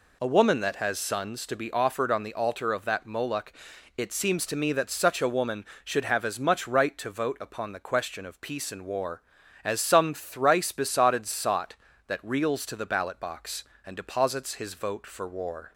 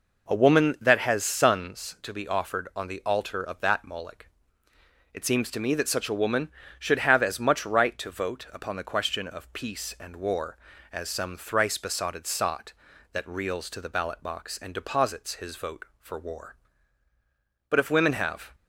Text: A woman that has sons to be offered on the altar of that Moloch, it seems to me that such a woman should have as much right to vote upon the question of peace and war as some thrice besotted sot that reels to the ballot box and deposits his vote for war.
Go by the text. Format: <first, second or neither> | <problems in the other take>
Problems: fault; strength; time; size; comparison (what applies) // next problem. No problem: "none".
first | goes on to say "But if women have"; noticeable; from 17.6 s on; 0.86 s long